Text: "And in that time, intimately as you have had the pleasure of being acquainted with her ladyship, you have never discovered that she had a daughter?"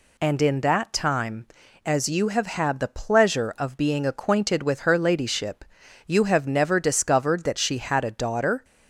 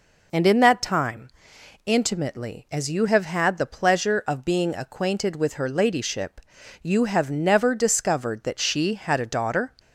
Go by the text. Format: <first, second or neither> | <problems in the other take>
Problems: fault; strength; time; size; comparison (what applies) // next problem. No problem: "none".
second | skips "intimately"; at 1.6 s